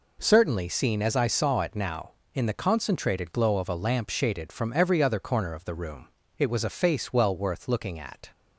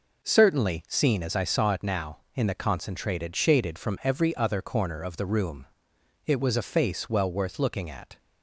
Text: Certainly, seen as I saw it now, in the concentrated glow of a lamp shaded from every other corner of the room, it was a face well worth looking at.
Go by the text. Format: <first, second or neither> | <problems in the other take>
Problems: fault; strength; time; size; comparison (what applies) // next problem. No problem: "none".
first | skips "glow of a lamp"; at 3.3 s